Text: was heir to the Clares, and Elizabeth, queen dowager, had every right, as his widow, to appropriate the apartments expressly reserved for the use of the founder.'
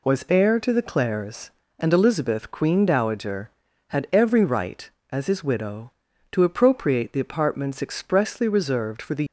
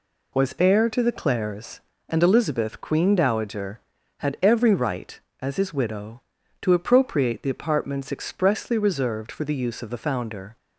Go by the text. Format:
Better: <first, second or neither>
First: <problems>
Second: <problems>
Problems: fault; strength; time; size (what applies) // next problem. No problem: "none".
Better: second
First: stops before "use of the founder"; at 9.2 s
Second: none